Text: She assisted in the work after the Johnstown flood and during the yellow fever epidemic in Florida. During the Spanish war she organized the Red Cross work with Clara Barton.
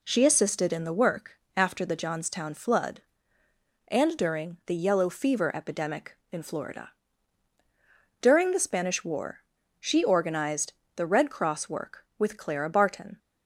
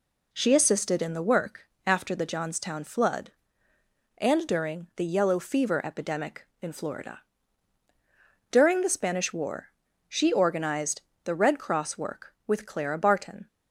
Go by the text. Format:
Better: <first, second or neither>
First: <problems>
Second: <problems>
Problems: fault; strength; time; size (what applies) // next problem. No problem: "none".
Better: neither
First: pauses between "work" and "after"; slight; at 1.3 s; 0.17 s long // pauses between "war" and "she"; at 9.3 s; 0.40 s long // pauses between "organized" and "the"; slight; at 10.7 s; 0.24 s long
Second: pauses between "work" and "after"; slight; at 1.6 s; 0.18 s long // pauses between "war" and "she"; at 9.6 s; 0.40 s long // pauses between "organized" and "the"; slight; at 11.0 s; 0.24 s long